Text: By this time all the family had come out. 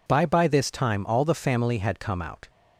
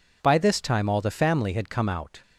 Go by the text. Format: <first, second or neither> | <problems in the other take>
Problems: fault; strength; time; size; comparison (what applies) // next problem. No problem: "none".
second | says "By" twice; at 0.2 s